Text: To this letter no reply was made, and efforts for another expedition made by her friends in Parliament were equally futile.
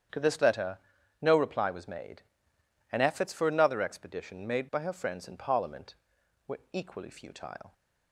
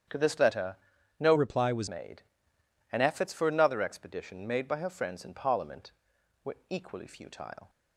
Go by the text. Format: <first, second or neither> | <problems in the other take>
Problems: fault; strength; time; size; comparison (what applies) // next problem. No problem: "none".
first | starts louder than the rest; strong; until 1.5 s; 8.5 dB; strong in the first // pauses between "letter" and "no"; at 0.7 s; 0.42 s long; also in the first // changes voice from "reply" to "was"; from 1.3 to 1.8 s; 0.5 s long